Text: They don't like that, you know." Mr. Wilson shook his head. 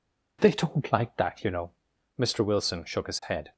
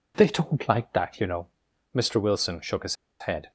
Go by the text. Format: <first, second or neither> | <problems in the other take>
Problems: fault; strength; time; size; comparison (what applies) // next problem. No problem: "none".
first | pauses between "his" and "head"; slight; at 2.9 s; 0.24 s long